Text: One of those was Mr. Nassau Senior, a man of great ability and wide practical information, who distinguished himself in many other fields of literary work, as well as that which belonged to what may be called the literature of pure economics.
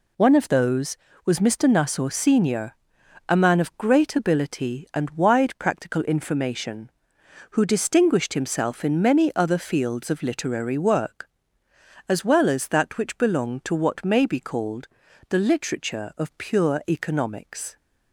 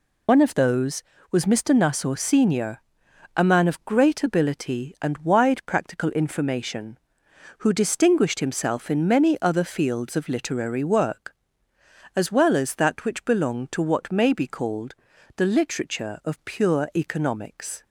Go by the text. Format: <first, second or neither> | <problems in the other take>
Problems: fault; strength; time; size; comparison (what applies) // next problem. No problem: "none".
first | loses the start of "One"; at 0.2 s; 60 ms // pauses between "called" and "the"; at 14.9 s; 0.40 s long; also in the first